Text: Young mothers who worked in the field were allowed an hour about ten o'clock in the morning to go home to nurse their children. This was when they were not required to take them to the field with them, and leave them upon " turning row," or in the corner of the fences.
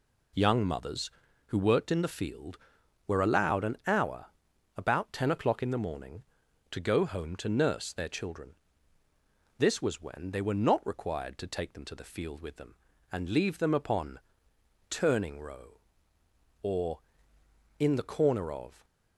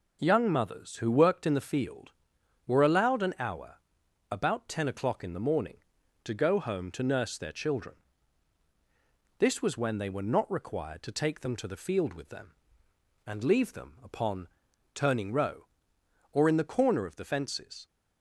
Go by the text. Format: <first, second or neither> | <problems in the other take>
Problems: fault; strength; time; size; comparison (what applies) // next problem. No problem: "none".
second | pauses between "hour" and "about"; noticeable; at 4.2 s; 0.50 s long; noticeable in the second // stops before "the fences"; at 18.8 s